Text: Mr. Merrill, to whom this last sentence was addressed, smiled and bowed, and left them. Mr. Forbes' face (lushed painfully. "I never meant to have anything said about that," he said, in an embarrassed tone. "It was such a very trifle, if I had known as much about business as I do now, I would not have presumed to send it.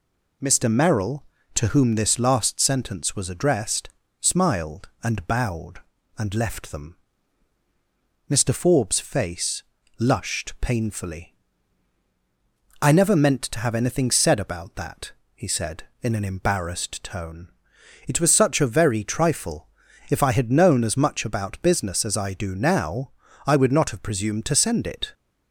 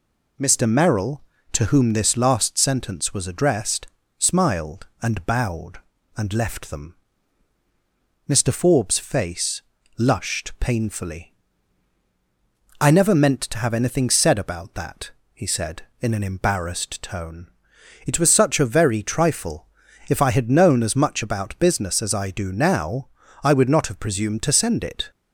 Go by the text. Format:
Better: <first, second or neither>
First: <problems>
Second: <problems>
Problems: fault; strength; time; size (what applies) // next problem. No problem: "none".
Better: neither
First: none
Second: none